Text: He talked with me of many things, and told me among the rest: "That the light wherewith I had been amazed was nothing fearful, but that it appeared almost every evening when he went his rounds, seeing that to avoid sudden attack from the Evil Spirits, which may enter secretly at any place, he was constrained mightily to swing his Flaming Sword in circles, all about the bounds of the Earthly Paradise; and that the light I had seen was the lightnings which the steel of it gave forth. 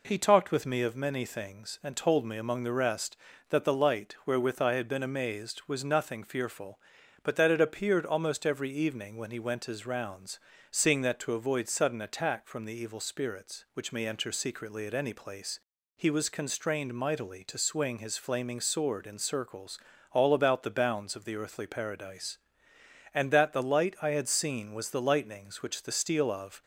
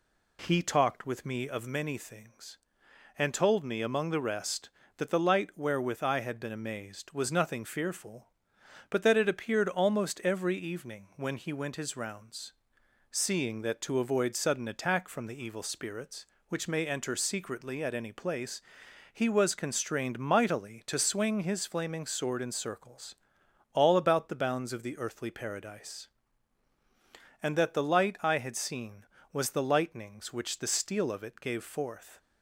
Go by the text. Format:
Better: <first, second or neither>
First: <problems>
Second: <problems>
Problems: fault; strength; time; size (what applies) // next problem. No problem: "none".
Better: second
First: stops before "it gave forth"; at 26.6 s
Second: none